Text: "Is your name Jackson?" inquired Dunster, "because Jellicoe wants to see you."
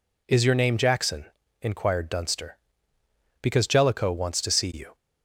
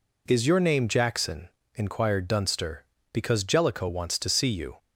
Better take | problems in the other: neither | none

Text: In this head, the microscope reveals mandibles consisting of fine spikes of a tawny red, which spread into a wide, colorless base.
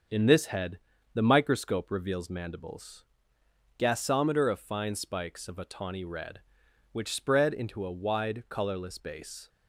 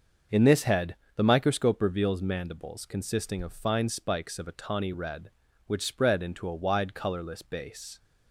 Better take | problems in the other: second | starts louder than the rest; until 1.4 s; 6.5 dB; also in the second // says "gasometer" for "consisting"; at 3.7 s

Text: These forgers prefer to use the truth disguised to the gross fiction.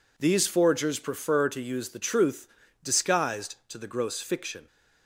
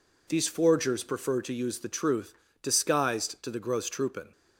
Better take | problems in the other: first | pauses between "truth" and "disguised"; slight; at 2.3 s; 0.28 s long; slight in the first // says "troopin" for "fiction"; at 3.8 s

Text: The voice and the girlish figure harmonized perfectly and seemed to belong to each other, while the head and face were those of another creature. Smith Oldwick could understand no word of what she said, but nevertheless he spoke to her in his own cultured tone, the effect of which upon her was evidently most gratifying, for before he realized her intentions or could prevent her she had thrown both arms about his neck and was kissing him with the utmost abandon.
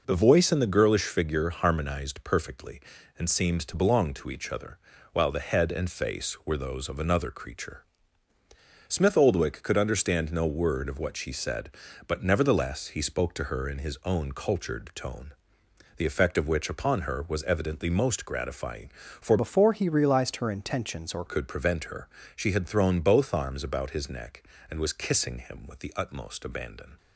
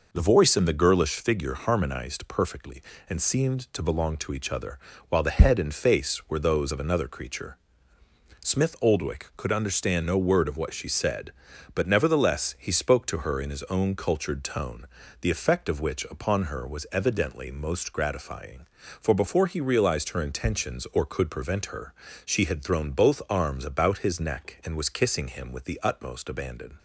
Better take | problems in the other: second | changes voice from "before" to "or"; from 19.3 to 21.2 s; 1.9 s long // pauses between "her" and "she"; slight; at 22.0 s; 0.26 s long; slight in the second

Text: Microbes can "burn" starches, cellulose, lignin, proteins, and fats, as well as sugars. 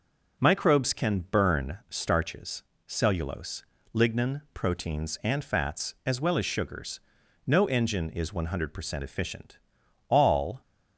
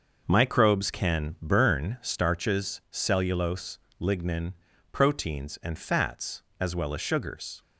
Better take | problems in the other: second | goes on to say "No engine is one hundred percent efficient All"; strong; from 7.4 s on; 3.1 s long

